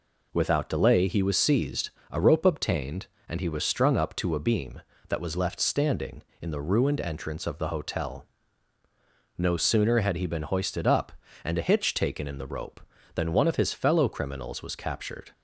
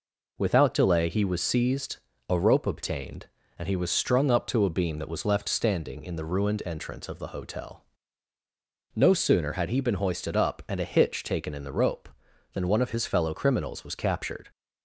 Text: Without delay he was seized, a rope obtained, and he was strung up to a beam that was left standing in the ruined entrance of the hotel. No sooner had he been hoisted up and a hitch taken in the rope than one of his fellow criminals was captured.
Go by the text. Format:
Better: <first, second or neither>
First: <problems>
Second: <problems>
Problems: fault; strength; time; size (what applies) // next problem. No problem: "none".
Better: neither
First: none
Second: none